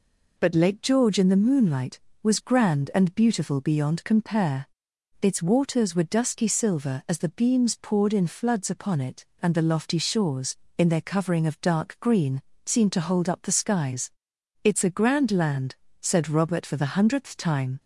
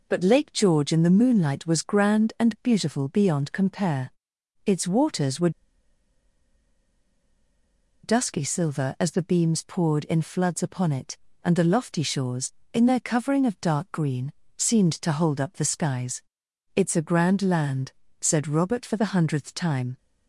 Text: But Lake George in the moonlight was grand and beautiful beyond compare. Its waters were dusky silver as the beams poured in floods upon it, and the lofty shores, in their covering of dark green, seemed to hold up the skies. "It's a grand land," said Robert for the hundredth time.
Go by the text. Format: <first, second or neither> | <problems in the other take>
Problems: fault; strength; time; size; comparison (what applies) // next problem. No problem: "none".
first | pauses between "were" and "dusky"; strong; at 5.4 s; 2.5 s long